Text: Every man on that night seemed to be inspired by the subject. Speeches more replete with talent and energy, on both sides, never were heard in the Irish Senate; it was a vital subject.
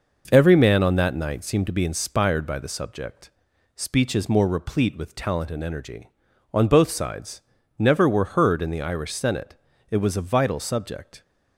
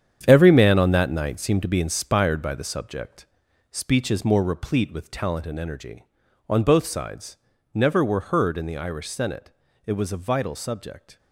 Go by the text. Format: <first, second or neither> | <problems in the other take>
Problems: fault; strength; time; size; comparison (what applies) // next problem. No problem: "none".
first | gets quieter; strong; throughout; 10 dB